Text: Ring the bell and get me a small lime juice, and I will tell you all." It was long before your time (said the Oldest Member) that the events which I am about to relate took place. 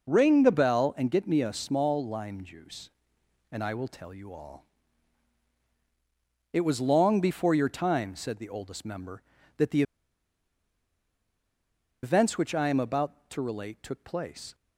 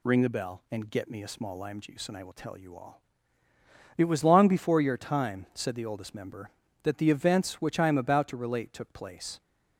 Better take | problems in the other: second | pauses between "the" and "events"; strong; at 9.8 s; 2.2 s long

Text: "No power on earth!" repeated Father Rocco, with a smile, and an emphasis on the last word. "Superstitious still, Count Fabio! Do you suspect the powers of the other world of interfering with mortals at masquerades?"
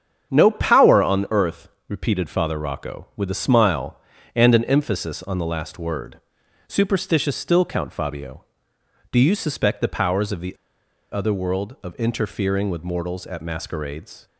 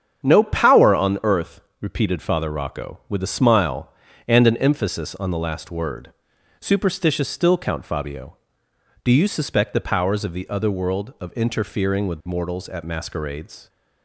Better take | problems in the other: second | starts louder than the rest; strong; until 1.3 s; 8 dB; strong in the second // pauses between "the" and "other"; noticeable; at 10.5 s; 0.55 s long

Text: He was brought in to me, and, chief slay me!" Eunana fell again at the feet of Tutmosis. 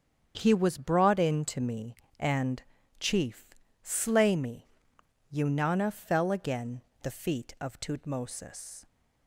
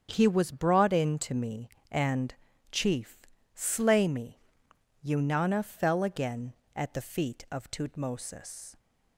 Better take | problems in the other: second | starts louder than the rest; strong; until 1.3 s; 8 dB; strong in the second // pauses between "chief" and "slay"; slight; at 3.5 s; 0.28 s long; slight in the second // skips "at"; at 6.9 s

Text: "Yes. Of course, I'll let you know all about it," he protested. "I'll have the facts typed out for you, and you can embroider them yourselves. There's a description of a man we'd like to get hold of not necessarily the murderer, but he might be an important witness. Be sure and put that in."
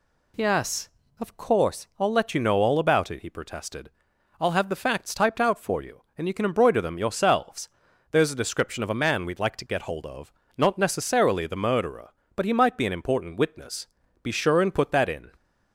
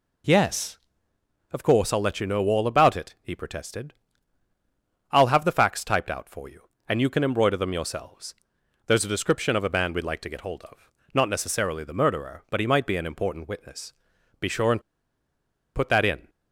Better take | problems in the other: first | pauses between "of" and "not"; slight; at 10.8 s; 0.24 s long; slight in the first // pauses between "and" and "put"; noticeable; at 14.8 s; 0.94 s long

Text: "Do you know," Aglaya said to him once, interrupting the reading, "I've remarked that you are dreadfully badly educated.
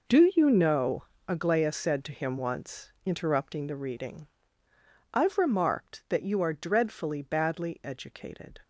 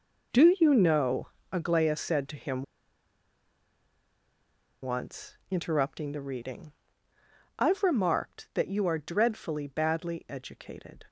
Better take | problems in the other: first | pauses between "him" and "once"; strong; at 2.6 s; 2.2 s long

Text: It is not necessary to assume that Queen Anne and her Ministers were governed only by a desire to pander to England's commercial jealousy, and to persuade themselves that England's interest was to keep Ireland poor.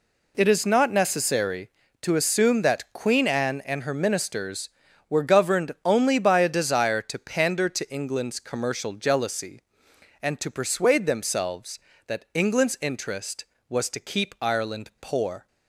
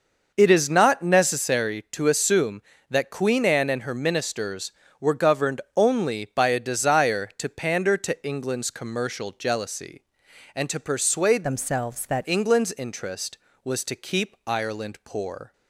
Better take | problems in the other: first | pauses between "governed" and "only"; slight; at 5.6 s; 0.16 s long // changes voice from "themselves" to "that"; from 11.4 to 12.2 s; 0.8 s long

